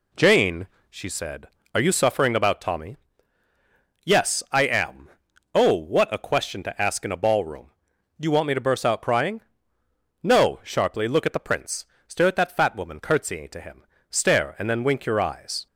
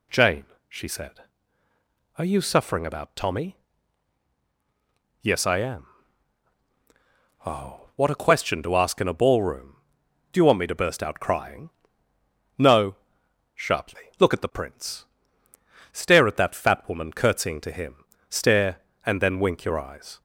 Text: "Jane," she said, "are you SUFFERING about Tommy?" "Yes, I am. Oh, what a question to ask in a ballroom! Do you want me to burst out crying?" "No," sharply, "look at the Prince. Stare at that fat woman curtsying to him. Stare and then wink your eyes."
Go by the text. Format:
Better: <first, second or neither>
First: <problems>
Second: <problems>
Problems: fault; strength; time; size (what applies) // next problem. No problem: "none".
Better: neither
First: none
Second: none